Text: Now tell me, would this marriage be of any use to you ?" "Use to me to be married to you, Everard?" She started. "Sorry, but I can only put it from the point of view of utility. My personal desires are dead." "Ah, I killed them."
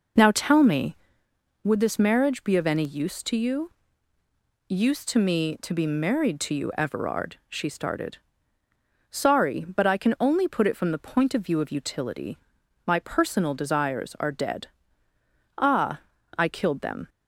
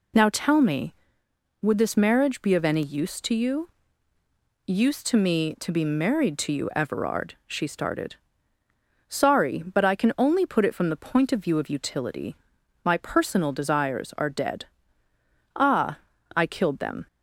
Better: second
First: starts louder than the rest; noticeable; until 1.7 s; 5.5 dB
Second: none

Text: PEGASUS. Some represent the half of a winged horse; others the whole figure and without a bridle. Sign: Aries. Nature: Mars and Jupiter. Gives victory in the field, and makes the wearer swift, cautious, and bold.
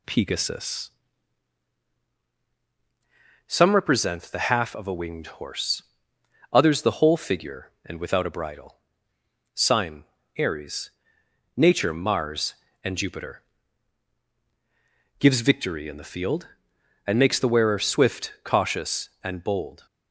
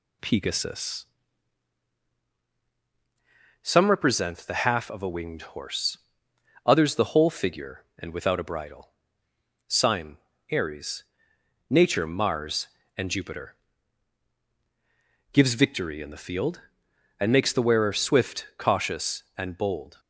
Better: neither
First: none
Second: none

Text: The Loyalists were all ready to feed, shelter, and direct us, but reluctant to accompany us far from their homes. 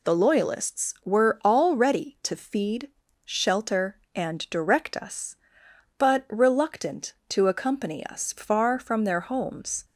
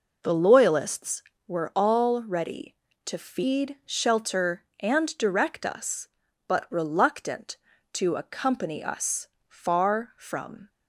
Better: first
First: none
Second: pauses between "us" and "far"; slight; at 9.2 s; 0.20 s long // stops before "their homes"; at 10.6 s

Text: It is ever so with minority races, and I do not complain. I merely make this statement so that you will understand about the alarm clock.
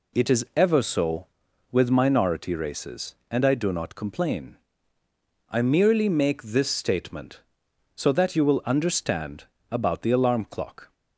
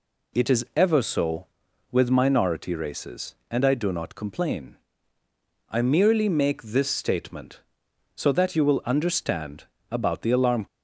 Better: first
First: pauses between "understand" and "about"; slight; at 9.4 s; 0.26 s long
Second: pauses between "understand" and "about"; slight; at 9.6 s; 0.26 s long // stops before "clock"; at 10.6 s

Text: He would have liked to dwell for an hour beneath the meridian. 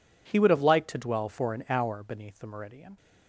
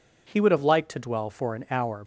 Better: first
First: none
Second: stops before "beneath the meridian"; at 2.0 s

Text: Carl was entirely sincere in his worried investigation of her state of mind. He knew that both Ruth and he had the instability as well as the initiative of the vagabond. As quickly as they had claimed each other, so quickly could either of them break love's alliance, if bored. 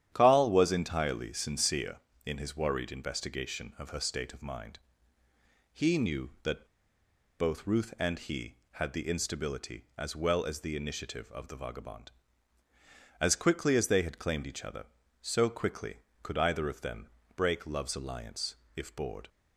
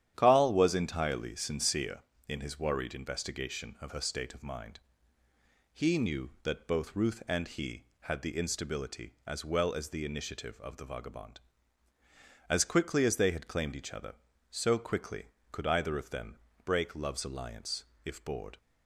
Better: second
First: starts louder than the rest; strong; until 1.1 s; 10.5 dB // pauses between "that" and "both"; noticeable; at 6.6 s; 0.71 s long // pauses between "them" and "break"; slight; at 17.0 s; 0.28 s long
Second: starts louder than the rest; strong; until 1.1 s; 10.5 dB // pauses between "them" and "break"; slight; at 16.3 s; 0.28 s long

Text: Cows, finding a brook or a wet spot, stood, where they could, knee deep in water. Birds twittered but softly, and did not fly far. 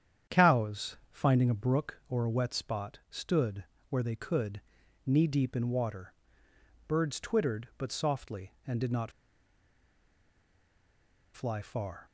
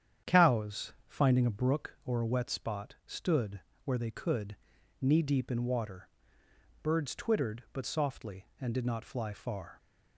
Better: second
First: starts louder than the rest; strong; until 1.4 s; 9 dB // pauses between "not" and "fly"; strong; at 9.1 s; 2.2 s long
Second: starts louder than the rest; strong; until 1.4 s; 9 dB

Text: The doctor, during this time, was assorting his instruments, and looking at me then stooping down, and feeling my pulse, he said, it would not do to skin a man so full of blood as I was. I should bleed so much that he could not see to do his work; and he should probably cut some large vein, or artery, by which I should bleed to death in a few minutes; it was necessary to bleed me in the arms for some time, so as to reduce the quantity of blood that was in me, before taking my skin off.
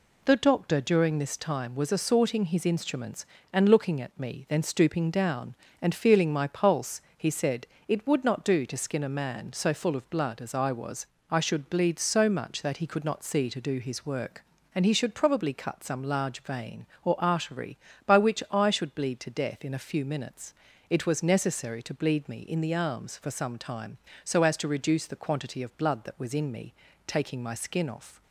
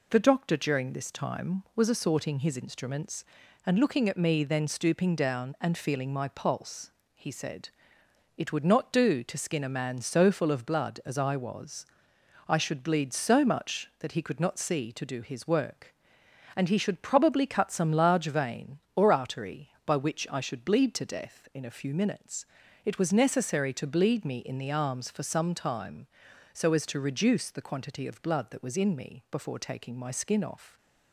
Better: second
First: skips "before"; at 26.9 s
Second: none

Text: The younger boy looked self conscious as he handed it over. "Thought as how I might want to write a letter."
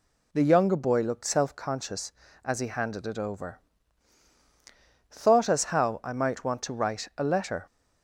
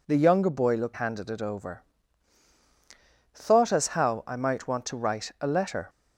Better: first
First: none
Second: skips "self conscious as he"; at 0.9 s

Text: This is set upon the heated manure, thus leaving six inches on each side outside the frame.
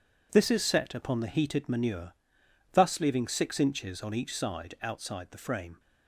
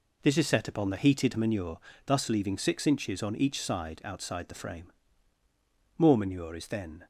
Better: first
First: none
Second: goes on to say "More manure is then"; noticeable; from 5.9 s on; 1.0 s long

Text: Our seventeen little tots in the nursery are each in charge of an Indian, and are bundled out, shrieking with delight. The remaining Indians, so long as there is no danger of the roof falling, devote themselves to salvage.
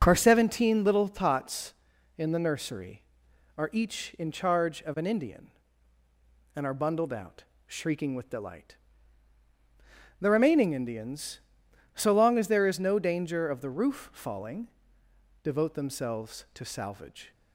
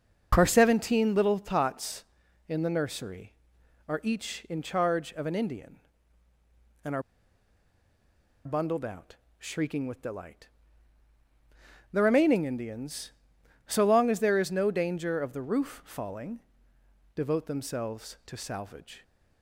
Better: first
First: none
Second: pauses between "are" and "bundled"; strong; at 7.0 s; 1.4 s long

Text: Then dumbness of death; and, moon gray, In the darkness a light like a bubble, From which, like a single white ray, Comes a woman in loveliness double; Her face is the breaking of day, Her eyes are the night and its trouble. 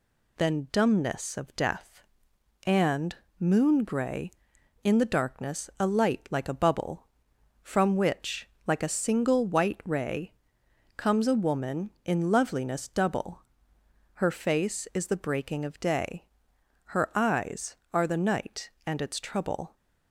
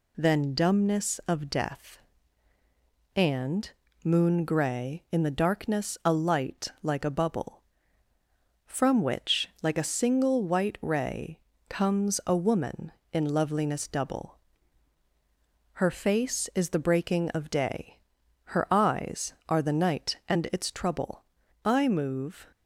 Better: first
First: none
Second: pauses between "light" and "like"; slight; at 6.6 s; 0.16 s long // goes on to say "I move"; noticeable; from 21.6 s on; 0.88 s long

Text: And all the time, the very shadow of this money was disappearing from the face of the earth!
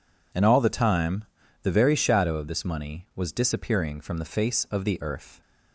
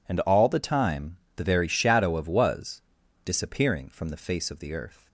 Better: first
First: none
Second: skips "this money"; at 2.2 s // pauses between "was" and "disappearing"; at 2.8 s; 0.42 s long

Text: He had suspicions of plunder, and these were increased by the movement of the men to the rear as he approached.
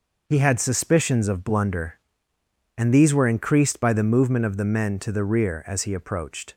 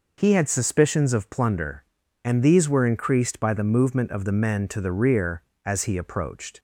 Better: second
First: says "blunder" for "plunder"; at 1.4 s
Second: none

